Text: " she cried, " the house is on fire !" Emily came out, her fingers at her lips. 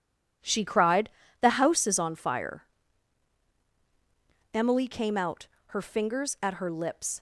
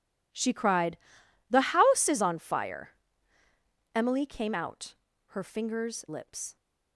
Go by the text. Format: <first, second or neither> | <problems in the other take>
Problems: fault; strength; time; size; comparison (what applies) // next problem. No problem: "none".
first | starts louder than the rest; strong; until 1.5 s; 8.5 dB; strong in the first // skips "at her"; at 6.0 s